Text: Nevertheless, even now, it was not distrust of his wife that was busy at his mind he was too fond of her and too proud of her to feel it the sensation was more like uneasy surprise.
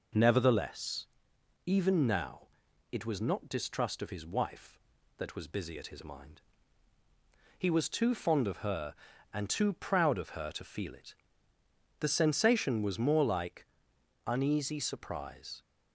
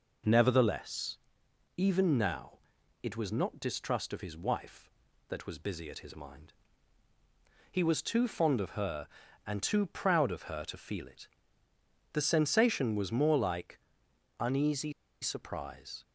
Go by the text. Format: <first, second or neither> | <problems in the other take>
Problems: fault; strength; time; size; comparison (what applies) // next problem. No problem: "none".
first | pauses between "mind" and "he"; at 6.5 s; 1.1 s long; also in the first // pauses between "it" and "the"; noticeable; at 11.2 s; 0.86 s long; noticeable in the first // pauses between "like" and "uneasy"; noticeable; at 13.7 s; 0.60 s long; noticeable in the first // pauses between "uneasy" and "surprise"; slight; at 14.9 s; 0.29 s long